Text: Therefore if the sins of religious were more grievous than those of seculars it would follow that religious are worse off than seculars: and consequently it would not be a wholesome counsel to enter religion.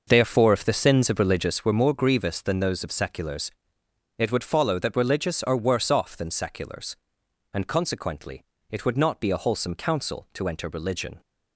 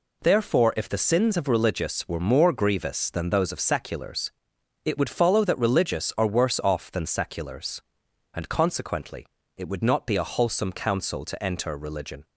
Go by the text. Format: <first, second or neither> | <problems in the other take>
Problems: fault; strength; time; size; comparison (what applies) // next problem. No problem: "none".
second | starts louder than the rest; noticeable; until 1.8 s; 6 dB // pauses between "seculars" and "it"; noticeable; at 3.5 s; 0.66 s long; noticeable in the second // pauses between "consequently" and "it"; slight; at 8.4 s; 0.28 s long; slight in the second